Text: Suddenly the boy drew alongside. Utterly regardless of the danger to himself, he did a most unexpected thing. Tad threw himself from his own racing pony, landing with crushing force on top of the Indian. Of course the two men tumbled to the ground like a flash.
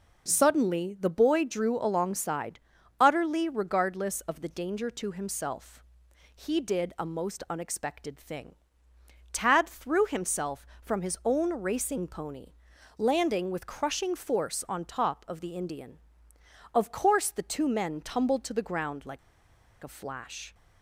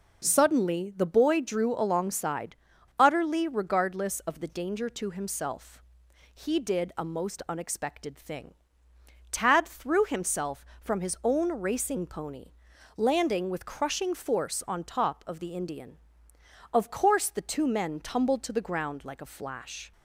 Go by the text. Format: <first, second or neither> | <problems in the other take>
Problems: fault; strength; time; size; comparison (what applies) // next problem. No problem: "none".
second | pauses between "like" and "a"; noticeable; at 19.1 s; 0.64 s long